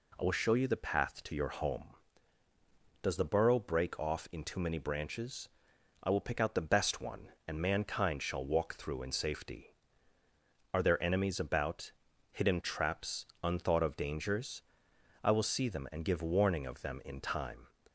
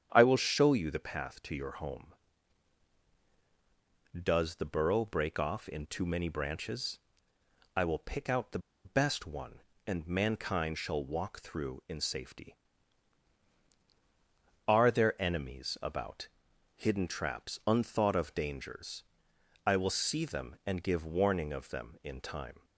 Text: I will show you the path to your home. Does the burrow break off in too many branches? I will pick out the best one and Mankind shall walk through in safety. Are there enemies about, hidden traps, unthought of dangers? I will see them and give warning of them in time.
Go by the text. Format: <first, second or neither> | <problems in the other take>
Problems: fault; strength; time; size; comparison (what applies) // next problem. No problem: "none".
first | starts louder than the rest; strong; until 1.1 s; 8.5 dB // pauses between "the" and "best"; slight; at 8.5 s; 0.26 s long